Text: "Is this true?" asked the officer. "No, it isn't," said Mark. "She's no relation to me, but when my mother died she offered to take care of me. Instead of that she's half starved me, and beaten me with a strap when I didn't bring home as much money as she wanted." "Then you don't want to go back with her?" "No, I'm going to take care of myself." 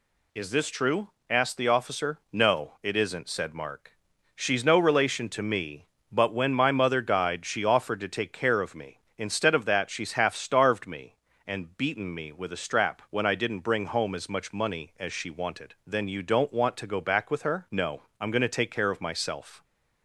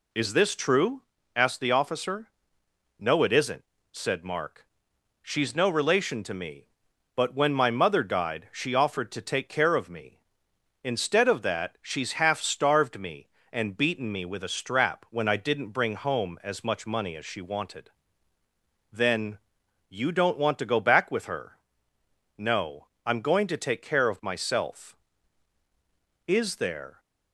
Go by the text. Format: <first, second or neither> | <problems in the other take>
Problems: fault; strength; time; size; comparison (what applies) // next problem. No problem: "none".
first | pauses between "Then" and "you"; noticeable; at 19.3 s; 0.50 s long // goes on to say "Is there"; noticeable; from 26.2 s on; 0.72 s long